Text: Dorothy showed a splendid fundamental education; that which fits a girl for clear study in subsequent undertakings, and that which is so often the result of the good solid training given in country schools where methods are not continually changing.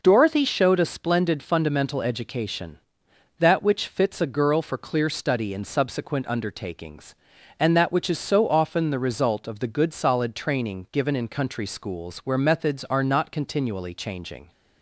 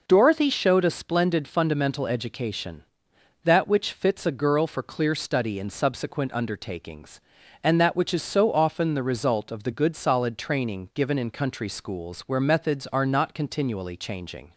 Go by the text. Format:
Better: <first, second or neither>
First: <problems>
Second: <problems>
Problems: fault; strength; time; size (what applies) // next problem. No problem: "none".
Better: neither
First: none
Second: none